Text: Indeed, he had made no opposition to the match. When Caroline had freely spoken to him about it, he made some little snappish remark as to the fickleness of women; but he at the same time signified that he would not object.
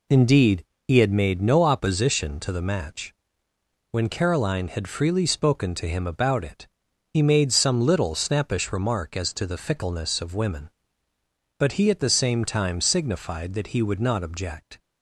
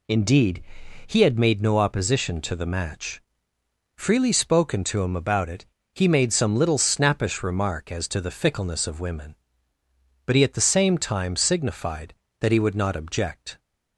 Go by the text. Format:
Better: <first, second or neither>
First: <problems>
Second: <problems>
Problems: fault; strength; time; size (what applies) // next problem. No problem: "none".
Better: first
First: none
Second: skips "When Caroline had"; at 3.5 s